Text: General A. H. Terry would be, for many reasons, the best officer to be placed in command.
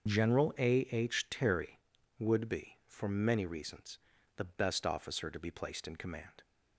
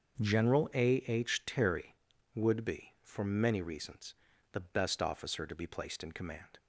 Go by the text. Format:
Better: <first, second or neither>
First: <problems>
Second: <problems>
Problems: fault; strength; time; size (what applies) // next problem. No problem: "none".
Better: second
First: loses the start of "General"; at 0.0 s; 65 ms // starts louder than the rest; until 1.0 s; 6 dB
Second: starts louder than the rest; until 1.2 s; 6.5 dB